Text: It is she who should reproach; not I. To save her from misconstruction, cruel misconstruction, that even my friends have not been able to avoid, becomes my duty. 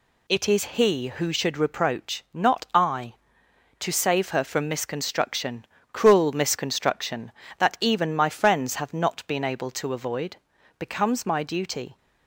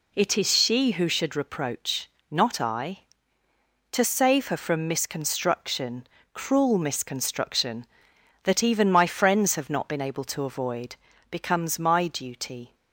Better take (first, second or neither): second